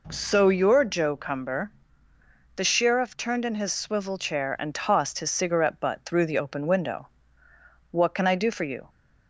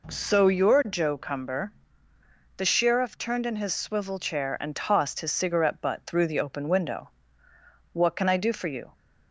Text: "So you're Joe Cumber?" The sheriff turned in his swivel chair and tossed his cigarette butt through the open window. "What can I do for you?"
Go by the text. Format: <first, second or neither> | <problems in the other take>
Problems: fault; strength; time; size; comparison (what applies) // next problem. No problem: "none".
neither | none